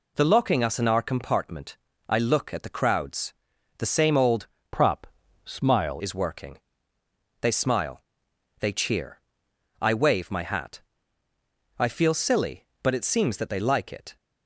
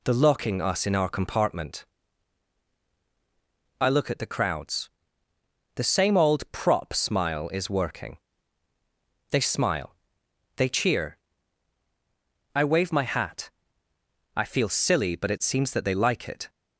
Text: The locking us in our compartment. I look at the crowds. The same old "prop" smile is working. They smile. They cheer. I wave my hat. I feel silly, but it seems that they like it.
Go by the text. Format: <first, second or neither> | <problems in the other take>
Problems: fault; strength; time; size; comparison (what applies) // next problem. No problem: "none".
second | changes voice from "prop" to "smile"; from 4.7 to 5.9 s; 1.2 s long // pauses between "prop" and "smile"; slight; at 5.0 s; 0.36 s long